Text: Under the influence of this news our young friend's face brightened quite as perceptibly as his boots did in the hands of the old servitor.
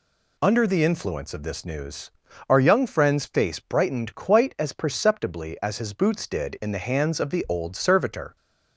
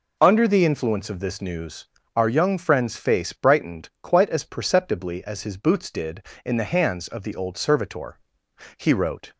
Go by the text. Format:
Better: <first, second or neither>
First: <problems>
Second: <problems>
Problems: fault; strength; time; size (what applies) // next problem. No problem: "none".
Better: first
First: pauses between "news" and "our"; slight; at 2.1 s; 0.36 s long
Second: pauses between "news" and "our"; slight; at 1.8 s; 0.30 s long // goes on to say "He wrote"; from 8.7 s on; 0.56 s long